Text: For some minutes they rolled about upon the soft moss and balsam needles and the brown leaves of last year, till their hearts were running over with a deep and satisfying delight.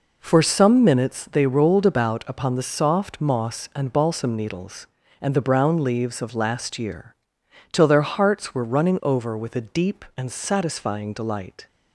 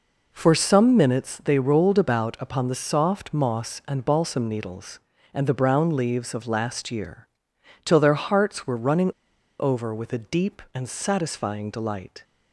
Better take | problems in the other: first | pauses between "running" and "over"; noticeable; at 9.1 s; 0.48 s long

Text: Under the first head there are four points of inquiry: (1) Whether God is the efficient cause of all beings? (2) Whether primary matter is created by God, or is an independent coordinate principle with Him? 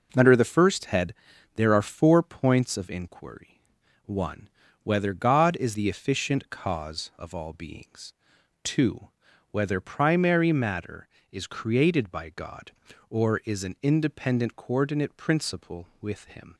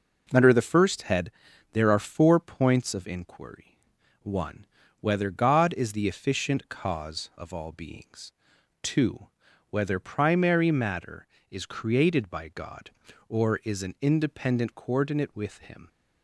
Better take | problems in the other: first | pauses between "head" and "there"; at 1.2 s; 0.42 s long; also in the first // skips "principle"; at 15.3 s

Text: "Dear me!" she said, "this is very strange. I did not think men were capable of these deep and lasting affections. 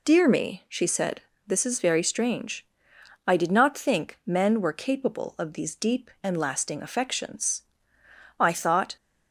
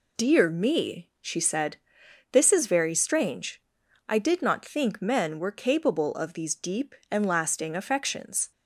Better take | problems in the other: second | goes on to say "I thought"; from 8.3 s on; 0.56 s long

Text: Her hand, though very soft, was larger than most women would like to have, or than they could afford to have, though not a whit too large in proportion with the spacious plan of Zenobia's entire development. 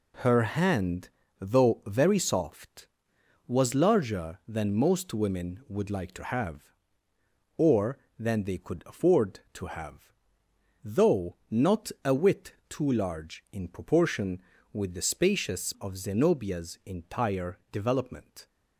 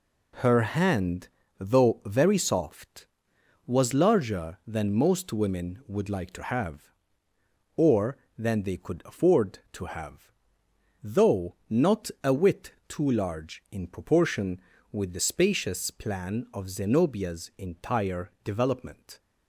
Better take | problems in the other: second | pauses between "though" and "not"; slight; at 11.3 s; 0.16 s long; slight in the second // pauses between "whit" and "too"; slight; at 12.5 s; 0.16 s long; slight in the second // skips "plan"; at 15.7 s

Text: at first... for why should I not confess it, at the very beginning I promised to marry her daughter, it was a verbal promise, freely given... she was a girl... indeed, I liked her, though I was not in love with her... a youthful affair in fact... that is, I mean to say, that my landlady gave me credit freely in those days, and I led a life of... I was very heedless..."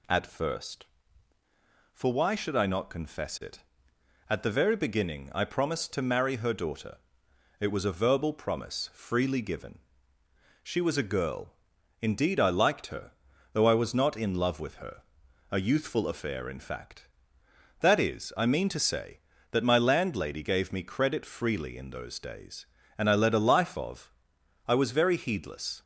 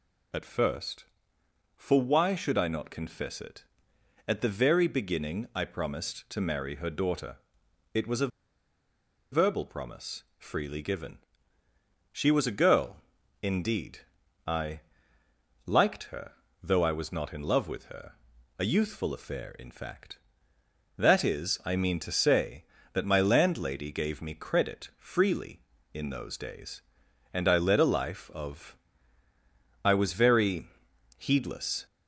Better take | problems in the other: first | pauses between "a" and "verbal"; at 8.2 s; 1.0 s long // pauses between "I" and "liked"; noticeable; at 14.7 s; 0.86 s long // pauses between "very" and "heedless"; noticeable; at 30.6 s; 0.54 s long

